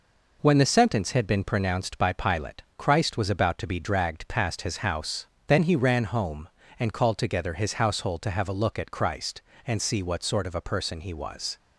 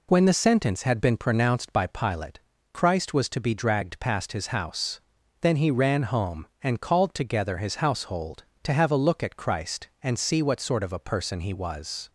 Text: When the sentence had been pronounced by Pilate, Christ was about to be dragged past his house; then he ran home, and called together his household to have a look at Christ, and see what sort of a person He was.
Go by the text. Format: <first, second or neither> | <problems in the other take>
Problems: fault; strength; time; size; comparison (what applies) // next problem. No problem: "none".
first | skips "about"; at 3.2 s